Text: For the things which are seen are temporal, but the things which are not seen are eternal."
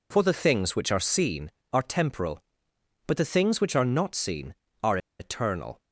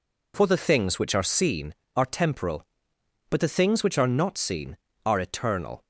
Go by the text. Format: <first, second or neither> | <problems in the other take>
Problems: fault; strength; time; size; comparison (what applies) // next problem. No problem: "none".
second | pauses between "are" and "eternal"; slight; at 4.9 s; 0.22 s long